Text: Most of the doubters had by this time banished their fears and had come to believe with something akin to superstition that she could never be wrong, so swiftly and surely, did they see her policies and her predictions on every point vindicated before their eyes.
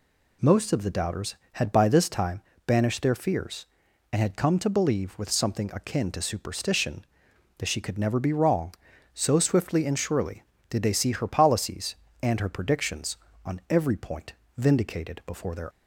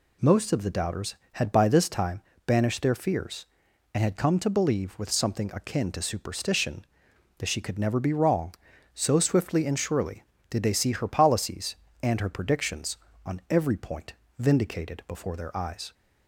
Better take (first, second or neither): second